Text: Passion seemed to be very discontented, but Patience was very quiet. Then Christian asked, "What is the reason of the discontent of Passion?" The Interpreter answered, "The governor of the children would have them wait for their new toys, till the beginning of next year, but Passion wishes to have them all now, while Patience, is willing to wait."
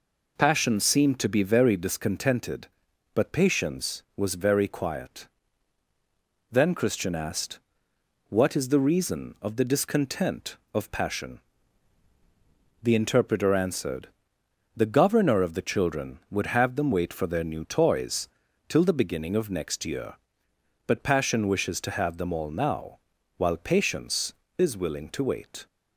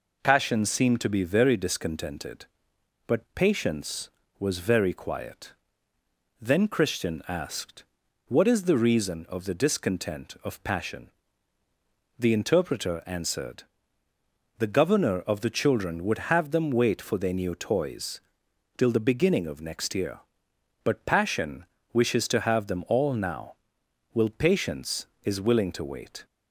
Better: first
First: none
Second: pauses between "Passion" and "wishes"; slight; at 21.6 s; 0.28 s long // says "will" for "while"; at 24.1 s

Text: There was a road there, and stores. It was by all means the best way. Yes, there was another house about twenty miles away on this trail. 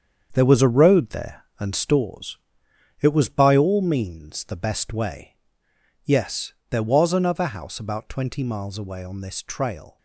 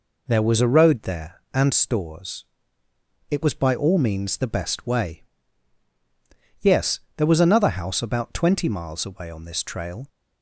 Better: second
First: gets quieter; strong; throughout; 8 dB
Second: none

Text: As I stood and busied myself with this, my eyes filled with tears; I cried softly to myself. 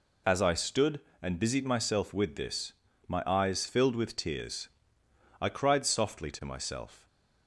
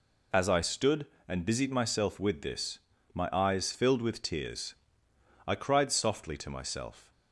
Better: neither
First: none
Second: none

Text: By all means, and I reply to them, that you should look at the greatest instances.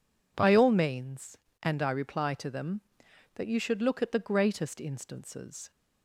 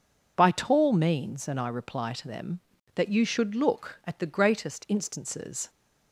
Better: first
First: none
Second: says "tall" for "all"; at 0.5 s

